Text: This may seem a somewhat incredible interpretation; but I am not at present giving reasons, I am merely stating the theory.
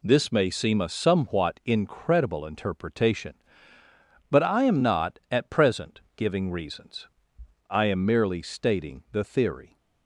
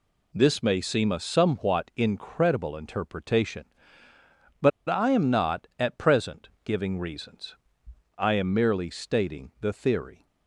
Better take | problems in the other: first | pauses between "but" and "I"; slight; at 4.7 s; 0.18 s long

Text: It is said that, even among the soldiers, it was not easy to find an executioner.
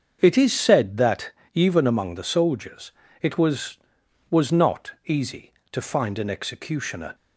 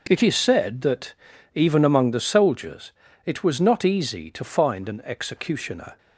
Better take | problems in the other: second | starts louder than the rest; until 1.2 s; 7 dB // says "was" twice; at 4.3 s // pauses between "not" and "easy"; slight; at 4.9 s; 0.16 s long

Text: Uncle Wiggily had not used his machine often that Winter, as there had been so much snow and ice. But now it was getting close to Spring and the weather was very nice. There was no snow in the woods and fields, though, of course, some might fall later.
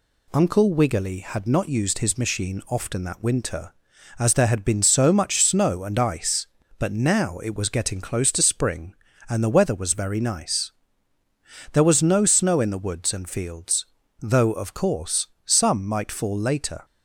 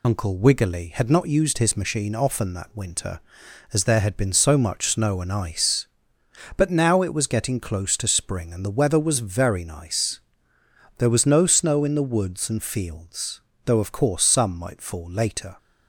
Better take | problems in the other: first | loses the start of "Uncle"; at 0.0 s; 85 ms

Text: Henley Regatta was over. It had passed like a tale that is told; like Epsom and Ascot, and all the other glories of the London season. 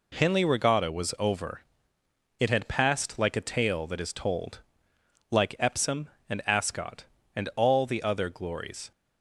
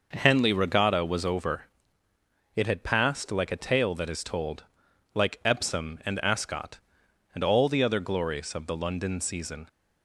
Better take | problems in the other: second | stops before "of the London season"; at 8.9 s

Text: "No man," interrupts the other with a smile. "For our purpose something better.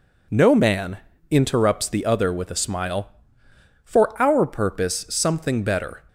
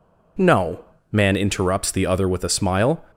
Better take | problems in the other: first | pauses between "No" and "man"; slight; at 0.8 s; 0.28 s long // stops before "For our purpose something better"; at 3.1 s

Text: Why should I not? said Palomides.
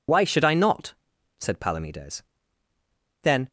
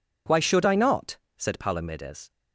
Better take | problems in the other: second | goes on to say "Then"; slight; from 3.2 s on; 0.28 s long

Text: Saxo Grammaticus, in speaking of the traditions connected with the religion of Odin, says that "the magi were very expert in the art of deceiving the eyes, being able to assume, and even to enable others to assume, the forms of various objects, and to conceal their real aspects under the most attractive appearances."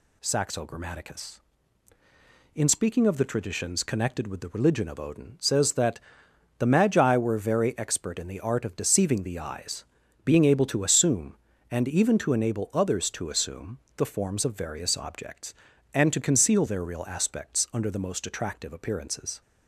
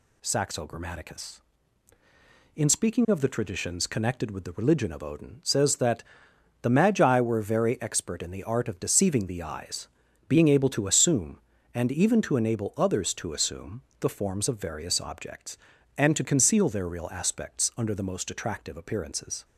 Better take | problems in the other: neither | pauses between "that" and "the"; noticeable; the same in both

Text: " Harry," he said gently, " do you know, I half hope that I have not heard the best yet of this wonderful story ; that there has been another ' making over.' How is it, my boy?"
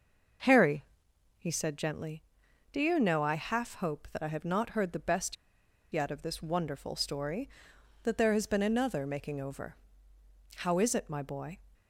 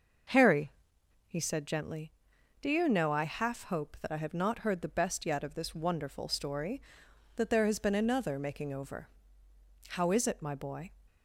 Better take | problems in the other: second | pauses between "best" and "yet"; noticeable; at 5.3 s; 0.58 s long

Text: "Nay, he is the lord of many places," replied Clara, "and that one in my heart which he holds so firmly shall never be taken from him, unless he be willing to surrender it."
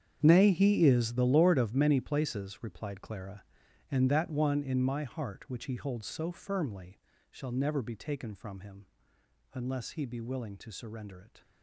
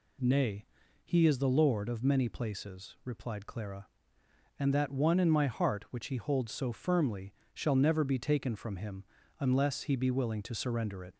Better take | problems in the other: second | gets quieter; strong; throughout; 15 dB // pauses between "firmly" and "shall"; slight; at 6.9 s; 0.32 s long; slight in the second

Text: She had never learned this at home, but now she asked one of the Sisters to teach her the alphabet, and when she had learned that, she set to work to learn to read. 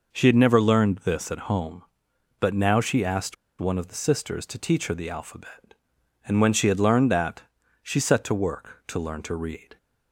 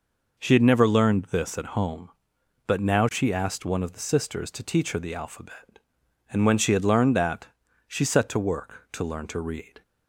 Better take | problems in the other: second | pauses between "asked" and "one"; slight; at 3.3 s; 0.25 s long

